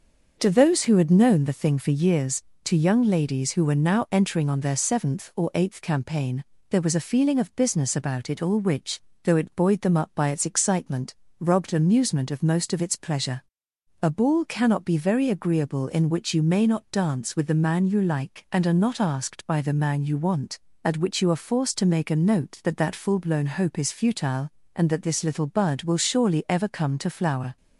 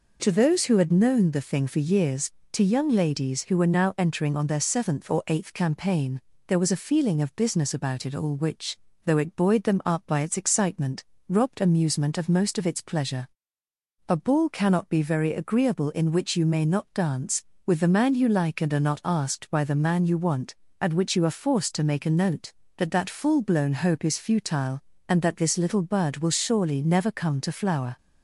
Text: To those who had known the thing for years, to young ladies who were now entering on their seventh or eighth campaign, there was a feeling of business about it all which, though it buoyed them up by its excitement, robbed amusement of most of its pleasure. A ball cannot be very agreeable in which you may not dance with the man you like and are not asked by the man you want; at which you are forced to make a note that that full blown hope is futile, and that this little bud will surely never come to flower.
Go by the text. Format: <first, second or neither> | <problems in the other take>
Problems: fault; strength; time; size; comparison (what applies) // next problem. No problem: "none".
second | starts louder than the rest; until 1.3 s; 6.5 dB // says "ever" for "never"; at 26.4 s